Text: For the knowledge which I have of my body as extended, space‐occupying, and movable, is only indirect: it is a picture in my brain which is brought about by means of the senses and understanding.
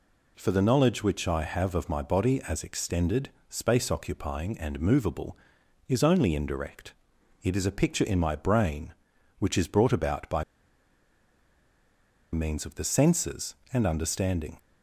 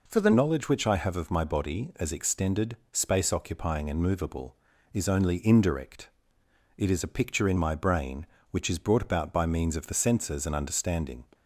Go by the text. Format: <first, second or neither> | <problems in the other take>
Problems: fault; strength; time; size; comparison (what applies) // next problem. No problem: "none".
second | pauses between "by" and "means"; strong; at 10.4 s; 1.8 s long